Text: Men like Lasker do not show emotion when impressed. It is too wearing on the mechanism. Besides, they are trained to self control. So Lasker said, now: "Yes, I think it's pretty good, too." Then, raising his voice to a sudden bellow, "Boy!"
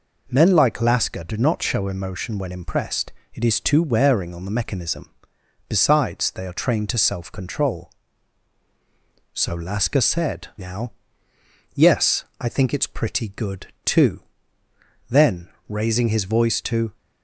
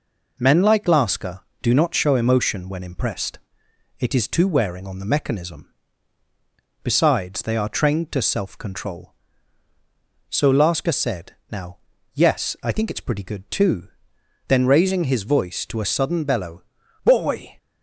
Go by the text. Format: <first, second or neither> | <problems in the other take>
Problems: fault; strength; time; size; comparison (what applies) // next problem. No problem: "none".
second | stops before "a sudden bellow Boy"; at 16.9 s